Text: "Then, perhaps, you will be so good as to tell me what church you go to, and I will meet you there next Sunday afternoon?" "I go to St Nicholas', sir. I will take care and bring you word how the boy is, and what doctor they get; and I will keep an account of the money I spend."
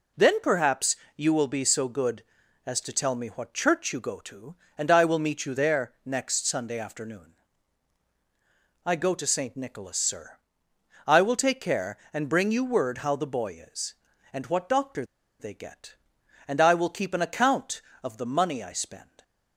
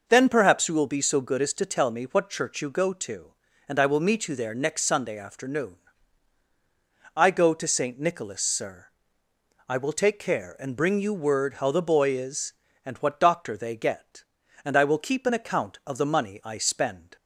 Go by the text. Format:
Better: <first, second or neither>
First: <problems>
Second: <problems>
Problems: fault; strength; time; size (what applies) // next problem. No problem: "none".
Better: second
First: pauses between "doctor" and "they"; slight; at 15.0 s; 0.36 s long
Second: none